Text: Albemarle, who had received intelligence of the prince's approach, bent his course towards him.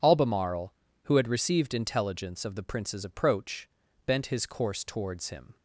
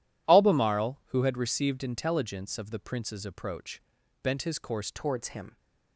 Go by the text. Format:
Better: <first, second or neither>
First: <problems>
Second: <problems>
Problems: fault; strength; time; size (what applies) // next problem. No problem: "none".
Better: first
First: none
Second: changes voice at "towards"; from 4.8 s on; 0.7 s long